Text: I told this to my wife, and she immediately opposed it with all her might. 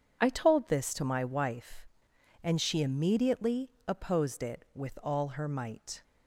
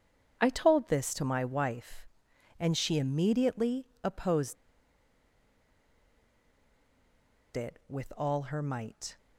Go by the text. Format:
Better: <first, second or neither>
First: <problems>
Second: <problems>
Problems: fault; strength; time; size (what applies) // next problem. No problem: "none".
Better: first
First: pauses between "immediately" and "opposed"; slight; at 3.7 s; 0.18 s long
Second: pauses between "immediately" and "opposed"; slight; at 3.8 s; 0.18 s long // pauses between "opposed" and "it"; strong; at 4.5 s; 2.9 s long